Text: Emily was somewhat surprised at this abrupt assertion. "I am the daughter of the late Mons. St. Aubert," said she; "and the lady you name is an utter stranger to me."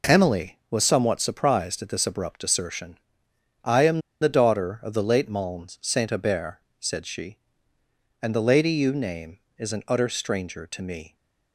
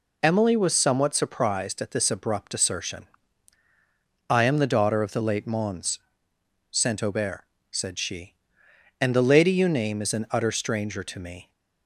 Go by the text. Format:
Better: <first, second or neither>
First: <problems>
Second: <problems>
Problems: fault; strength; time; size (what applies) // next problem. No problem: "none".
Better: second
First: pauses between "am" and "the"; slight; at 4.0 s; 0.20 s long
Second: none